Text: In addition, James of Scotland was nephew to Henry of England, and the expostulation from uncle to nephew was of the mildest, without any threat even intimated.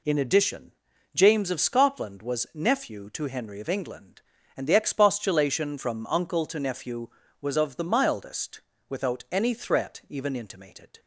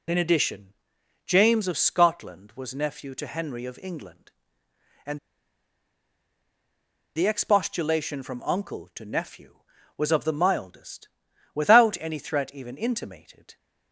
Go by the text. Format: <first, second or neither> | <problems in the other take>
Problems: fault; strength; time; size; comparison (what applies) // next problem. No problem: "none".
first | pauses between "and" and "the"; strong; at 5.1 s; 1.9 s long